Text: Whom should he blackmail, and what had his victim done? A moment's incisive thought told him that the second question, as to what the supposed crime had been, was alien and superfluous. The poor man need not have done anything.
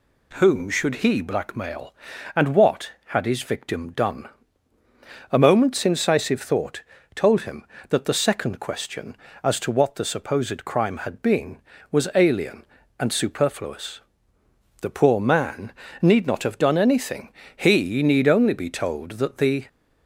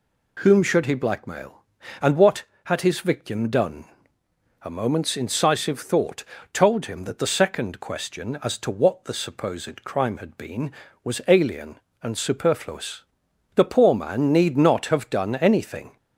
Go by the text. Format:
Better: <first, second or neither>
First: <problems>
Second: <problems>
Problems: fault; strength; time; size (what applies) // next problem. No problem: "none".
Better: second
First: pauses between "thought" and "told"; slight; at 6.8 s; 0.32 s long // pauses between "man" and "need"; slight; at 15.7 s; 0.28 s long // goes on to say "He need only be told that the"; strong; from 17.5 s on; 2.1 s long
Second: pauses between "thought" and "told"; slight; at 6.2 s; 0.30 s long